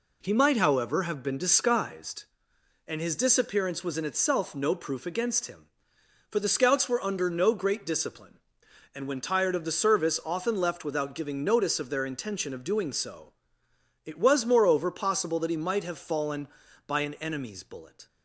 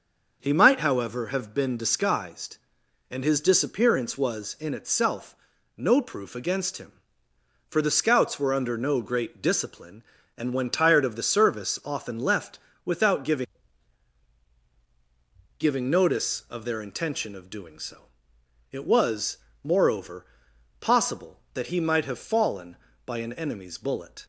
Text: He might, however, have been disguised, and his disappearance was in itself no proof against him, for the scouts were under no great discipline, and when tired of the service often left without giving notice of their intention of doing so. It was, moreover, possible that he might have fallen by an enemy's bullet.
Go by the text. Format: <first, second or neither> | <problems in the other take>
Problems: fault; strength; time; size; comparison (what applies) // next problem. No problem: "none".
first | starts louder than the rest; until 1.4 s; 6.5 dB // pauses between "itself" and "no"; at 5.3 s; 0.42 s long // pauses between "left" and "without"; slight; at 12.5 s; 0.28 s long // says "giving" twice; at 15.5 s